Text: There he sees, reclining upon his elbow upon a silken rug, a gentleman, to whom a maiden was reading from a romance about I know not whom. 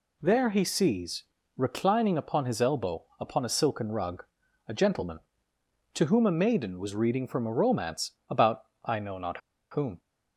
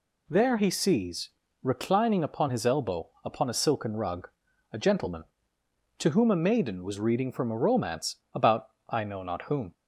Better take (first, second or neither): second